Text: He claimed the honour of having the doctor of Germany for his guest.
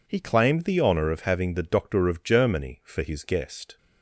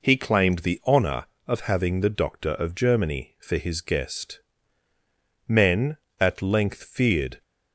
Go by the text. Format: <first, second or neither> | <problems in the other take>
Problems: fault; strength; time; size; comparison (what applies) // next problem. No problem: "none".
first | goes on to say "Men at length feared"; strong; from 5.4 s on; 1.9 s long